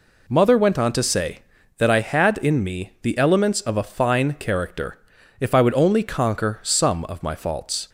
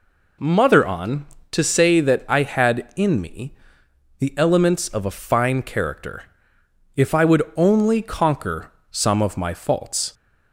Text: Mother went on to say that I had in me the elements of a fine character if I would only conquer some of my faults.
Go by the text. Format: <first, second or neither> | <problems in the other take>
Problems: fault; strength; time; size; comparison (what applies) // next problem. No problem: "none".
first | skips "went"; at 0.8 s // pauses between "me" and "the"; noticeable; at 3.5 s; 0.66 s long // pauses between "character" and "if"; noticeable; at 6.2 s; 0.72 s long; also in the first // pauses between "would" and "only"; slight; at 7.4 s; 0.16 s long // pauses between "conquer" and "some"; slight; at 8.7 s; 0.18 s long